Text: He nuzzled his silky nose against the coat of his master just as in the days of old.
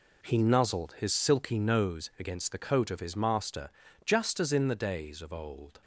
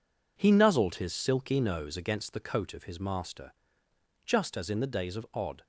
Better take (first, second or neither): first